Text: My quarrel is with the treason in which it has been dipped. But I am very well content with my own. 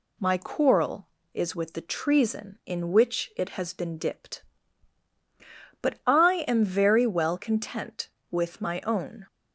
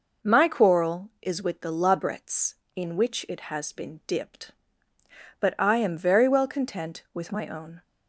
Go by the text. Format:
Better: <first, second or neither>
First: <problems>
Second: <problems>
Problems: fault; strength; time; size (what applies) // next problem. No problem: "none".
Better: first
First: none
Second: says "labrets" for "treason"; at 1.7 s